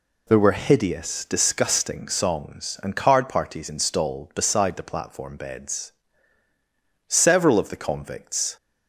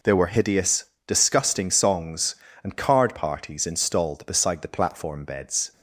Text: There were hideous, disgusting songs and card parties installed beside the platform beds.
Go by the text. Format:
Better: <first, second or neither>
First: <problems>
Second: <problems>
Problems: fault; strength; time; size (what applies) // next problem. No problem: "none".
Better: second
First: goes on to say "Several of the convicts"; from 7.0 s on; 1.4 s long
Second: none